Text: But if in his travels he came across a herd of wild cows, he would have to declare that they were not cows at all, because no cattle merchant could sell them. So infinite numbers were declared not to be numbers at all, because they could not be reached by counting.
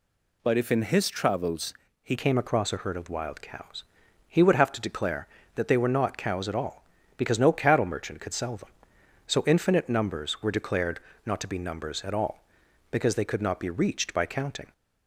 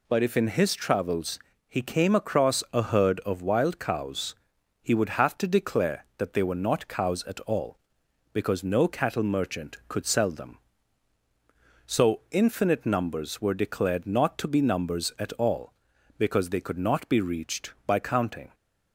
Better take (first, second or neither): second